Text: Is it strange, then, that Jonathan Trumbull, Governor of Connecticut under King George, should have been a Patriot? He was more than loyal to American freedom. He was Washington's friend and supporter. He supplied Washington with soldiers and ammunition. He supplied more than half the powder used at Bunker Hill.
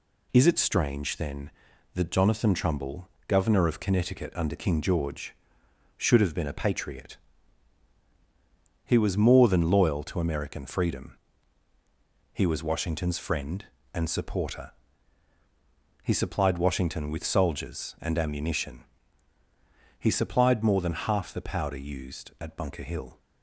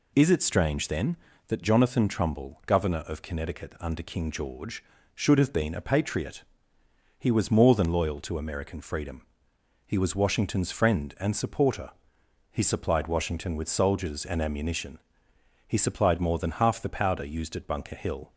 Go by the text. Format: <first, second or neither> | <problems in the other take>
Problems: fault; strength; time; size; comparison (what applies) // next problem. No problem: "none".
neither | none